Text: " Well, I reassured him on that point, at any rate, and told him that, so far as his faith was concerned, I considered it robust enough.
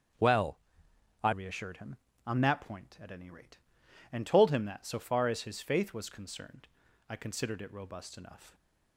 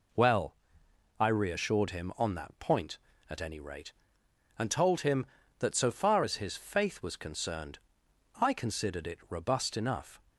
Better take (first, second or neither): second